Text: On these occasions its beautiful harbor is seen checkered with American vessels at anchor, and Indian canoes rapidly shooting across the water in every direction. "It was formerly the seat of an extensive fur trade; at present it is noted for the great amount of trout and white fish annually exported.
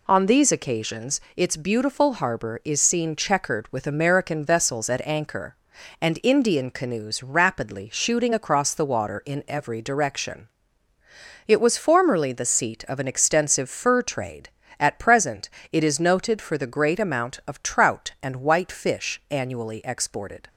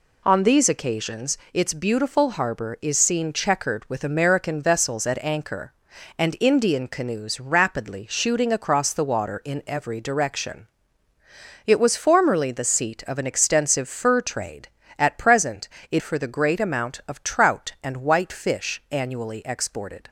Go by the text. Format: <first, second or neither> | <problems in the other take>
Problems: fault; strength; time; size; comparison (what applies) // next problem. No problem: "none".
first | pauses between "occasions" and "its"; slight; at 1.3 s; 0.16 s long; slight in the first // pauses between "present" and "it"; slight; at 15.6 s; 0.20 s long; slight in the first // skips "is noted"; at 16.0 s